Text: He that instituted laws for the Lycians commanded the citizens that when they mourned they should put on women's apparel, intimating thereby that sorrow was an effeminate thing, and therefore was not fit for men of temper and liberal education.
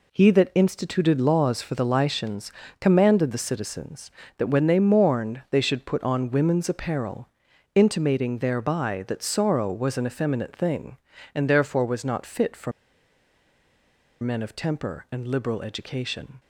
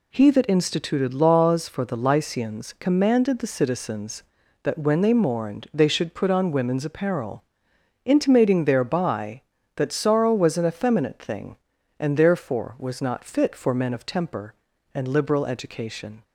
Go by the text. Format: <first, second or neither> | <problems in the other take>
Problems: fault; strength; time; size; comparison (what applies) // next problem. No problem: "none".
second | pauses between "Lycians" and "commanded"; slight; at 2.5 s; 0.30 s long // pauses between "for" and "men"; strong; at 12.7 s; 1.5 s long